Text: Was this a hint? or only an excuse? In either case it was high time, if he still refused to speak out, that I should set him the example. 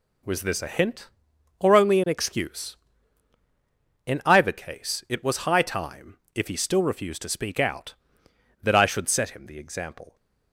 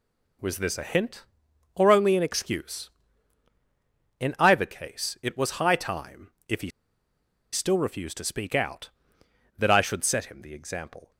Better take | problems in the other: first | pauses between "he" and "still"; noticeable; at 6.6 s; 0.83 s long

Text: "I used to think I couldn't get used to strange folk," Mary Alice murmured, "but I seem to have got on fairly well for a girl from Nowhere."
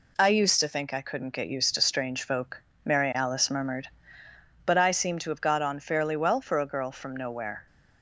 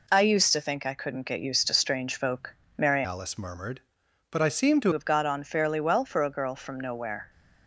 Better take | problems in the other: first | changes voice from "Alice" to "to"; from 3.0 to 4.9 s; 1.9 s long

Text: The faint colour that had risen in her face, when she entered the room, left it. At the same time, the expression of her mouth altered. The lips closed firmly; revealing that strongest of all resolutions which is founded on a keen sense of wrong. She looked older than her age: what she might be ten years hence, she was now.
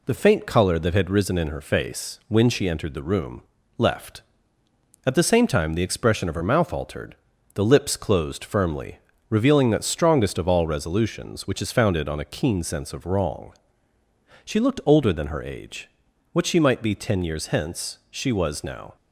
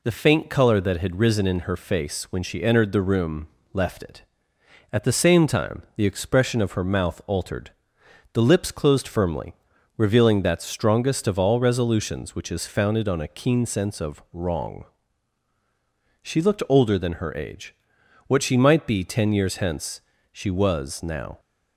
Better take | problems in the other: second | skips "it"; at 4.6 s

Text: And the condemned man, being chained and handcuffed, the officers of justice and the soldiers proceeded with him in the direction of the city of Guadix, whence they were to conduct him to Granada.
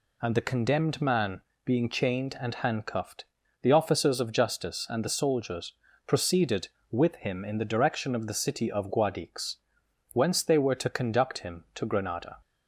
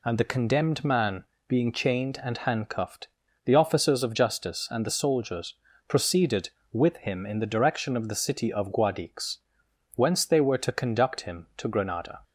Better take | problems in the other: neither | pauses between "soldiers" and "proceeded"; slight; the same in both

